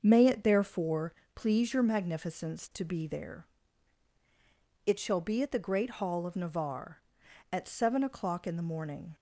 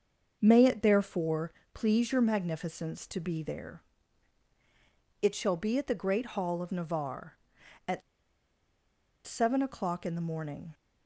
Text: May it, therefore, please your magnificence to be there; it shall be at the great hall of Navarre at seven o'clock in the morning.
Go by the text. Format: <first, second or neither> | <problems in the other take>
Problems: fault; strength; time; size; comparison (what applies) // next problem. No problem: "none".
first | starts louder than the rest; until 1.4 s; 6.5 dB; also in the first // pauses between "at" and "seven"; strong; at 8.0 s; 1.2 s long